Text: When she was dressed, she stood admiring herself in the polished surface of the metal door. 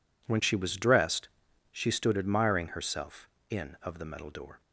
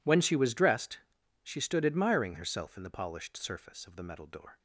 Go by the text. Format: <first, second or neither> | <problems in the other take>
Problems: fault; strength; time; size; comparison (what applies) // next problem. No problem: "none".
second | skips "the polished surface"; at 3.7 s